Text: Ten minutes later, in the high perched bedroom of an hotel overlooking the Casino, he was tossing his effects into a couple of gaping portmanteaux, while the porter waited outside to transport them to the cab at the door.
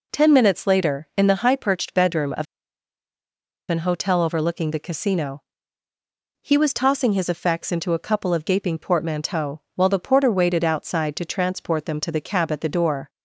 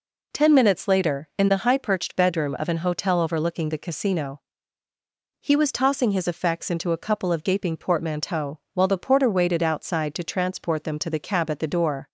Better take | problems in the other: second | pauses between "of" and "an"; at 2.4 s; 1.2 s long

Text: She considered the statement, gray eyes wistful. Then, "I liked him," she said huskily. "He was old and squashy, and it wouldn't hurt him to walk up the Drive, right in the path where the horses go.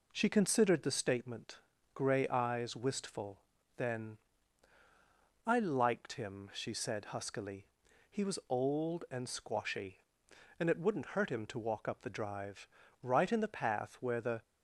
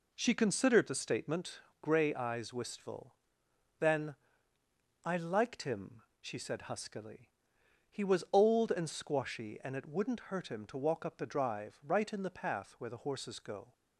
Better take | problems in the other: second | stops before "horses go"; at 14.4 s

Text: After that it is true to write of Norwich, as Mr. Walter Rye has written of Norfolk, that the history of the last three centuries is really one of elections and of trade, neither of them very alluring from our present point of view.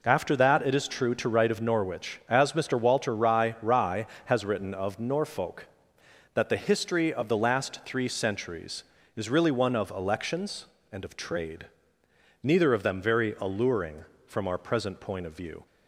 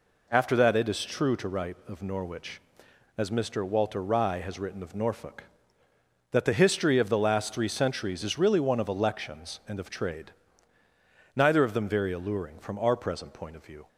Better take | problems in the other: second | says "Rye" twice; at 3.6 s

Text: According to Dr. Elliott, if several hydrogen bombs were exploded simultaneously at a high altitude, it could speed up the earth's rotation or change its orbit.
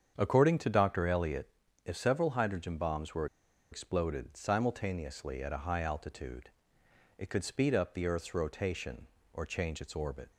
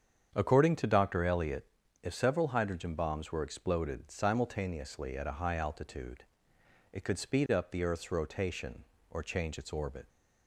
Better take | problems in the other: second | starts louder than the rest; strong; until 1.1 s; 8 dB; strong in the second // pauses between "were" and "exploded"; noticeable; at 3.2 s; 0.45 s long

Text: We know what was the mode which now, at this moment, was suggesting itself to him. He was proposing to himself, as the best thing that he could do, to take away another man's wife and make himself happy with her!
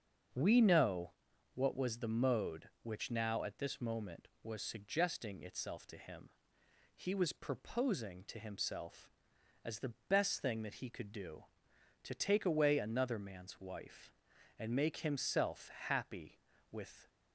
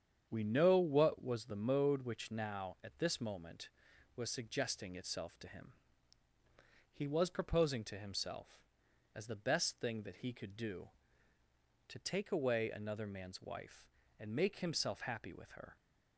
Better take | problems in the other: second | starts louder than the rest; until 1.7 s; 6.5 dB; strong in the second // pauses between "know" and "what"; at 1.1 s; 0.44 s long // pauses between "the" and "best"; slight; at 9.9 s; 0.16 s long // pauses between "himself" and "happy"; slight; at 15.7 s; 0.18 s long // stops before "her"; at 17.0 s

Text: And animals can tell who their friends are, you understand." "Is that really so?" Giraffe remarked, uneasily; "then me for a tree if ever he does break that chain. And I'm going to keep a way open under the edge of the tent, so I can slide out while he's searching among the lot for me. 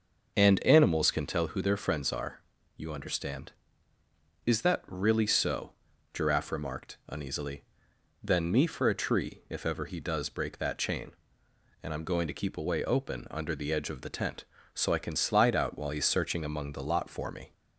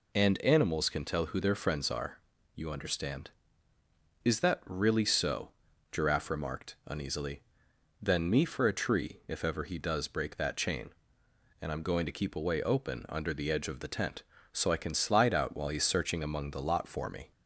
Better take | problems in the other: second | starts louder than the rest; noticeable; until 1.5 s; 6 dB

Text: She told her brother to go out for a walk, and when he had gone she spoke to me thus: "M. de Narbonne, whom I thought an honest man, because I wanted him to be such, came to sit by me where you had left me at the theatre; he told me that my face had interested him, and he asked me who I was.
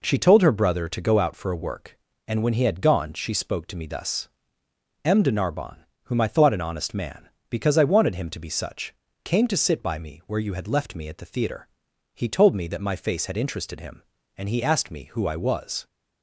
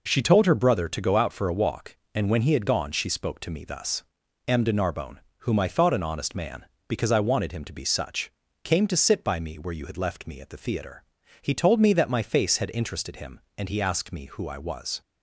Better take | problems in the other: second | says "work" for "walk"; at 1.5 s

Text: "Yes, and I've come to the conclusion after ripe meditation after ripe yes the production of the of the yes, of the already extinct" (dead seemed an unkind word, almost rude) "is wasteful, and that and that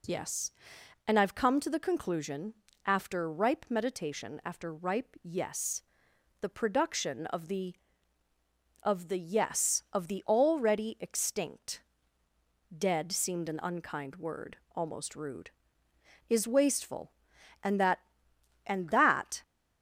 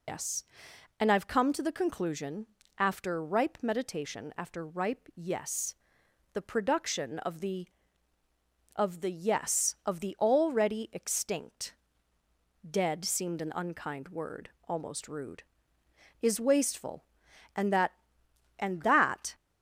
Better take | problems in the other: first | loses the start of "Yes"; at 0.0 s; 115 ms // pauses between "conclusion" and "after"; slight; at 2.4 s; 0.32 s long; slight in the first // pauses between "yes" and "the"; noticeable; at 5.7 s; 0.60 s long; noticeable in the first

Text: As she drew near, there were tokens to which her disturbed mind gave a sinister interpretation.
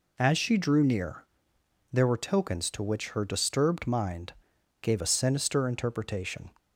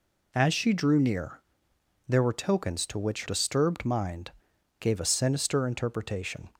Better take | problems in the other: first | skips "her"; at 3.2 s // pauses between "mind" and "gave"; noticeable; at 4.3 s; 0.48 s long; noticeable in the first

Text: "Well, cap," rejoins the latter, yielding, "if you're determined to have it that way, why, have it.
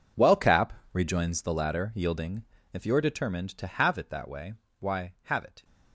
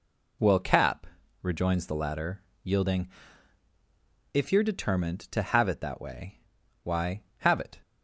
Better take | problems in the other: second | gets quieter; strong; throughout; 17 dB

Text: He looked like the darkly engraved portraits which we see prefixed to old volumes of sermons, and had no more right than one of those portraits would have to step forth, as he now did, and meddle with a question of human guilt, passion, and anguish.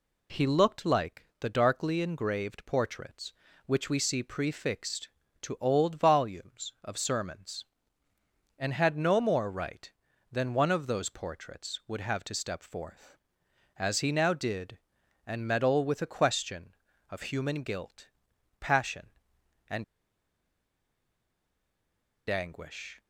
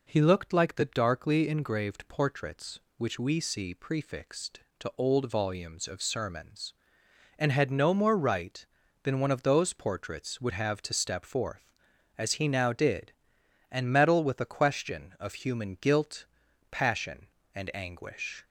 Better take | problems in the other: second | pauses between "and" and "anguish"; strong; at 19.8 s; 2.4 s long

